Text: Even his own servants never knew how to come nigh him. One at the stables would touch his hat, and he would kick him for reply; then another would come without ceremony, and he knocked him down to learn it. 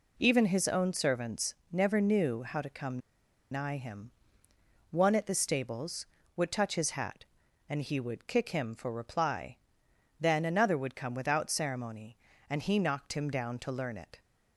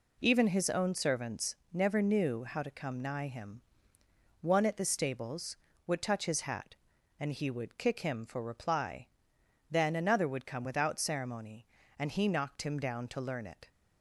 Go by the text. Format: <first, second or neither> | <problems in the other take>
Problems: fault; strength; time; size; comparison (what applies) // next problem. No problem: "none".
second | pauses between "servants" and "never"; slight; at 1.5 s; 0.18 s long; slight in the second // pauses between "come" and "nigh"; noticeable; at 2.9 s; 0.52 s long